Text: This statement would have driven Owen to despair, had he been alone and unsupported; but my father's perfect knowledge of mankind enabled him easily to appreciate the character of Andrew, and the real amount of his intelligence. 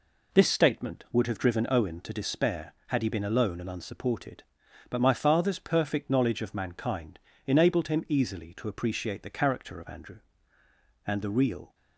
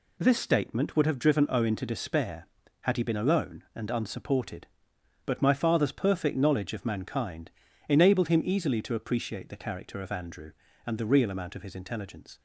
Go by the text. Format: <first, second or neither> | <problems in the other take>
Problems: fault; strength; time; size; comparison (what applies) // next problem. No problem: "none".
second | pauses between "mankind" and "enabled"; slight; at 7.1 s; 0.28 s long; slight in the second // stops before "amount of his intelligence"; at 11.7 s